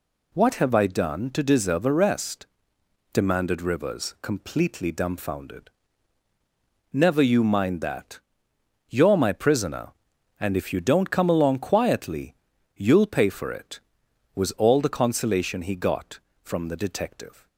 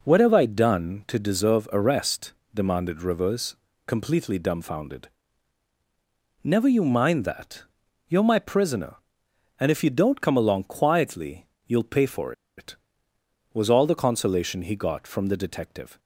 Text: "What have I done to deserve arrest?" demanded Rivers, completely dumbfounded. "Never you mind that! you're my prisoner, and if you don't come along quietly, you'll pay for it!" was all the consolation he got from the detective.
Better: first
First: none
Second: pauses between "for" and "it"; slight; at 12.3 s; 0.24 s long

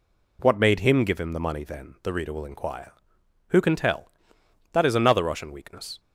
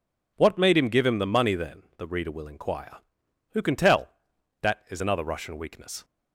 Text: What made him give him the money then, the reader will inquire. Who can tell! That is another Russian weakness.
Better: neither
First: none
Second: none

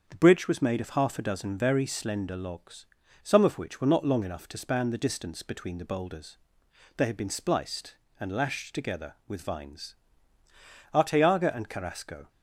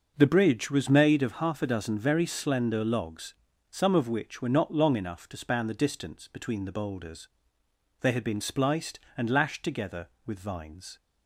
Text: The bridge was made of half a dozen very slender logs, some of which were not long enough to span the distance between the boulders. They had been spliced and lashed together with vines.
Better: second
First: starts louder than the rest; until 1.0 s; 7 dB // goes on to say "Arteaga and Carrasco"; from 10.9 s on; 1.3 s long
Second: starts louder than the rest; noticeable; until 1.1 s; 6 dB

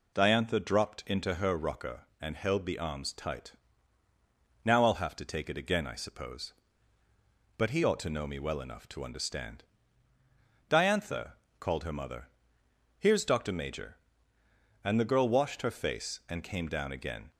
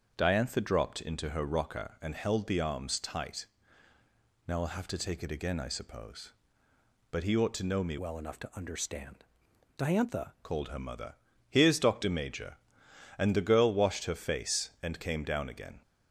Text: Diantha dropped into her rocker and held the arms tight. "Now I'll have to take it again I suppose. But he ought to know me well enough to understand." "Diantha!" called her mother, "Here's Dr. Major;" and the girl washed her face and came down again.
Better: first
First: none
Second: starts louder than the rest; until 1.1 s; 7 dB // changes voice from "well" to "Diantha"; from 7.9 to 10.3 s; 2.4 s long

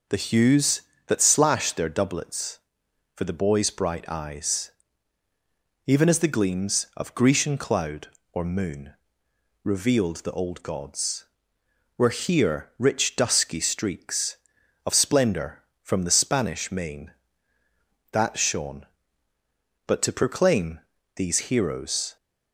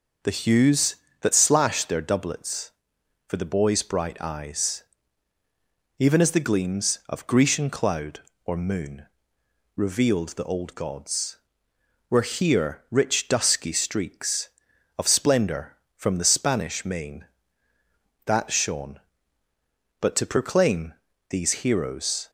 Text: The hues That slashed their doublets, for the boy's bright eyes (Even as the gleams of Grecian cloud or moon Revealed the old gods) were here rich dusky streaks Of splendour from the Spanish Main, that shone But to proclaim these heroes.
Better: neither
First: pauses between "moon" and "Revealed"; noticeable; at 8.9 s; 0.70 s long // pauses between "proclaim" and "these"; slight; at 20.8 s; 0.36 s long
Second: pauses between "moon" and "Revealed"; noticeable; at 9.0 s; 0.70 s long // pauses between "proclaim" and "these"; slight; at 20.9 s; 0.36 s long

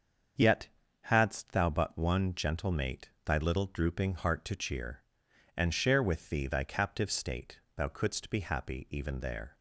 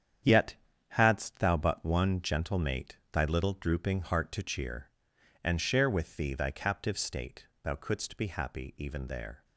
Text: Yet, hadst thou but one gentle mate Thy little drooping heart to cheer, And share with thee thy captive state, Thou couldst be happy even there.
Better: first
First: starts louder than the rest; until 1.6 s; 7 dB // pauses between "mate" and "Thy"; slight; at 3.0 s; 0.16 s long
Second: gets quieter; strong; throughout; 8.5 dB // starts louder than the rest; strong; until 1.5 s; 8.5 dB // pauses between "mate" and "Thy"; slight; at 2.9 s; 0.16 s long

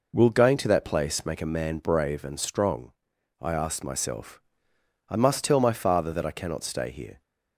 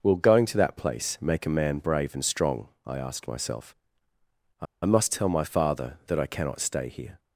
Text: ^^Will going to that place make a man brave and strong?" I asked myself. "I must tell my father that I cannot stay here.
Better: first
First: none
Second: pauses between "I" and "must"; slight; at 4.6 s; 0.19 s long

